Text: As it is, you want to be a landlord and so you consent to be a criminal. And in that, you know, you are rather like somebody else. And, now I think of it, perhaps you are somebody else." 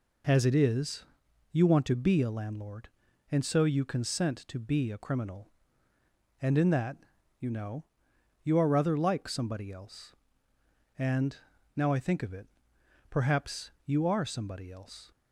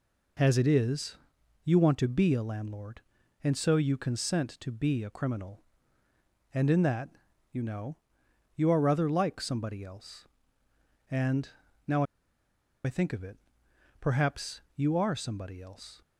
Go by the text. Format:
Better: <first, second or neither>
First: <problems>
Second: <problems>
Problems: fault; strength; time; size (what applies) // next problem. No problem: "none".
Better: first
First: none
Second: pauses between "now" and "I"; noticeable; at 12.0 s; 0.80 s long